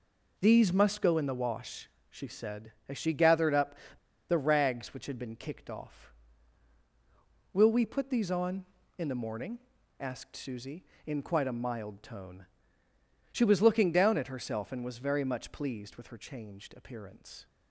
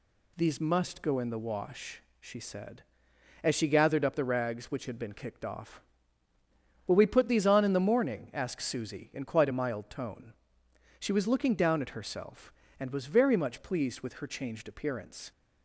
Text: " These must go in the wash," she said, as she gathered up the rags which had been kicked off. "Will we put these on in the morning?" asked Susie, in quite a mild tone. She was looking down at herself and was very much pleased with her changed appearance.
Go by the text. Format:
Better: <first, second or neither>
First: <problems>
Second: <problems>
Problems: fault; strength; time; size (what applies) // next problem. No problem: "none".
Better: second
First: pauses between "up" and "the"; noticeable; at 3.7 s; 0.55 s long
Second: none